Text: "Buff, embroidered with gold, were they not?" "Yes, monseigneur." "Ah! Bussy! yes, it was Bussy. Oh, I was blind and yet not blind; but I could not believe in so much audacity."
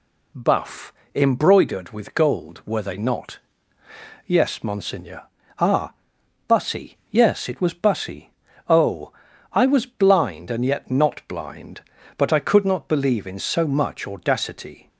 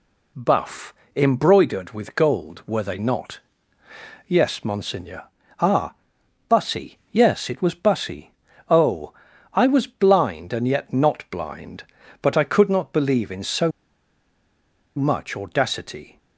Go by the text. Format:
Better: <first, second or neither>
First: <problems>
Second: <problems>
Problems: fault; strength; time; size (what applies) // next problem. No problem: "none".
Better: first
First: none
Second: pauses between "so" and "much"; strong; at 13.7 s; 1.2 s long